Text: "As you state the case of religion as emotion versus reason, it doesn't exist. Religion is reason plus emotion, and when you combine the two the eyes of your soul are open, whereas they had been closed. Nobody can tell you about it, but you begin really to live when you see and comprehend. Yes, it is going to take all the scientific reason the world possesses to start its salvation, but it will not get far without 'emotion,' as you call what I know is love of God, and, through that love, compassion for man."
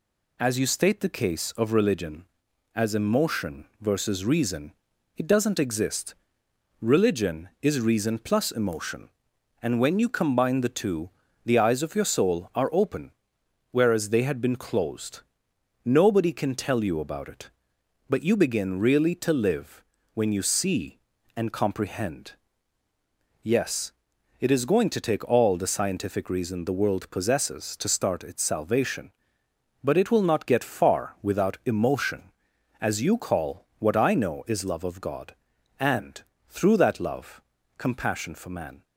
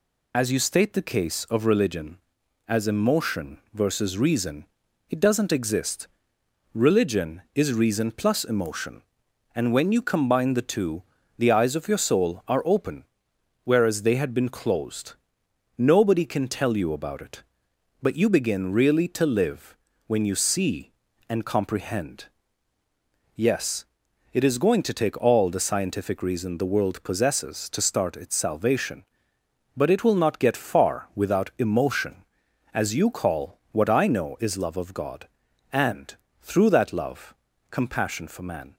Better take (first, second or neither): first